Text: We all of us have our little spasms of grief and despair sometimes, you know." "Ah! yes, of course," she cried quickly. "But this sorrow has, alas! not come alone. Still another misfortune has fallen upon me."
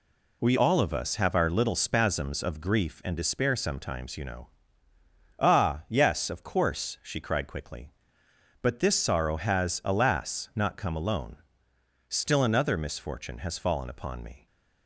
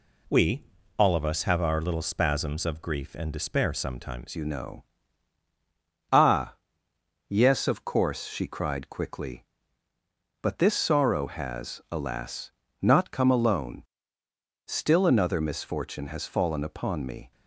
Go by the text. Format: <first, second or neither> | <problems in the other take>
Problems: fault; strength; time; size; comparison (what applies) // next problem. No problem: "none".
first | pauses between "We" and "all"; slight; at 0.6 s; 0.34 s long // changes voice at "you"; from 4.3 s on; 13.0 s long